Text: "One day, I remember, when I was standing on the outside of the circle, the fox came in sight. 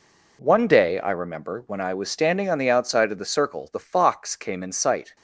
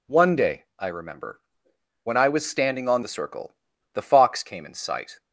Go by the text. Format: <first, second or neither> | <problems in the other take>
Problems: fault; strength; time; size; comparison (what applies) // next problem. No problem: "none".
first | skips "the outside of"; at 3.0 s